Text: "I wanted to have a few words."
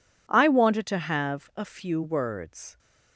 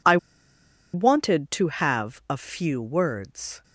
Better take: first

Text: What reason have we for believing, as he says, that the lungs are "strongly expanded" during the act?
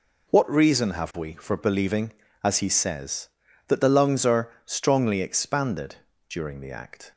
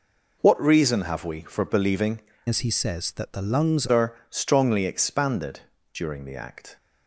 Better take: first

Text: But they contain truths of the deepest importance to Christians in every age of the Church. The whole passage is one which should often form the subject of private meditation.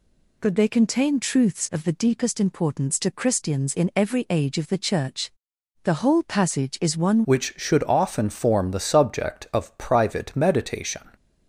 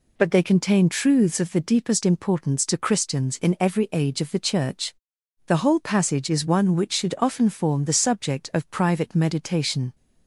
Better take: second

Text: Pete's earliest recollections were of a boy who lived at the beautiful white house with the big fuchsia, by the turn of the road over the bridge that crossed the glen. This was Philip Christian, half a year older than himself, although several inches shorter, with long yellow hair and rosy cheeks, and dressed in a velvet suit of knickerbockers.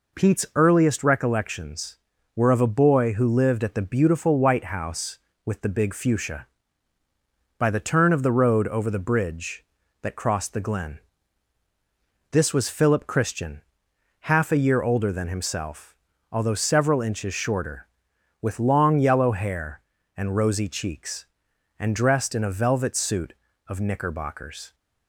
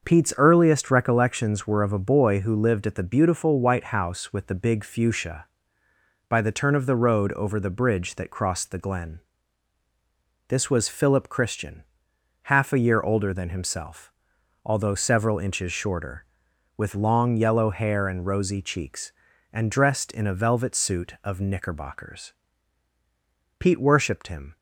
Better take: first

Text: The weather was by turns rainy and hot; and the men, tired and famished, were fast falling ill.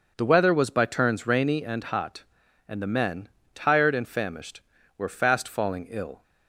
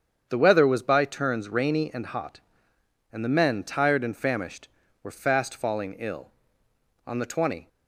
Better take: first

